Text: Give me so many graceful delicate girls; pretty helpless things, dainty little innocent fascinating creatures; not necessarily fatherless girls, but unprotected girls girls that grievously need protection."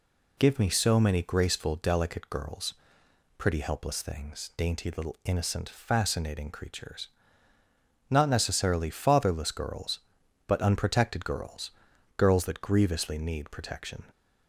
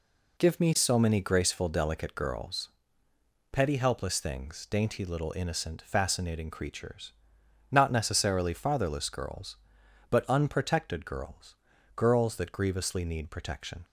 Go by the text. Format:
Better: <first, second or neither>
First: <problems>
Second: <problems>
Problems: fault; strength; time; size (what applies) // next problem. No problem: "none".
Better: first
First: pauses between "girls" and "girls"; noticeable; at 11.7 s; 0.46 s long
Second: says "petty" for "pretty"; at 3.5 s // pauses between "girls" and "girls"; at 11.5 s; 0.40 s long